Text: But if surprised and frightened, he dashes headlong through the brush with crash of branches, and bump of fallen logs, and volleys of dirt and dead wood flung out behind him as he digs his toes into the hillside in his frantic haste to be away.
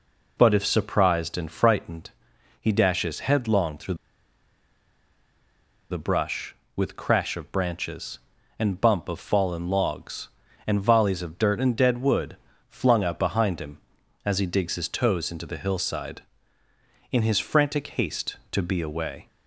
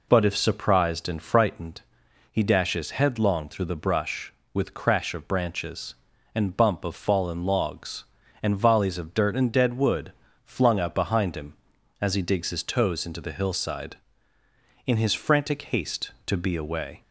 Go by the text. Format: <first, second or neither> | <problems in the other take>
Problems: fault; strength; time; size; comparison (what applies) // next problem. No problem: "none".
second | pauses between "through" and "the"; strong; at 3.9 s; 1.9 s long // pauses between "wood" and "flung"; slight; at 12.3 s; 0.32 s long; slight in the second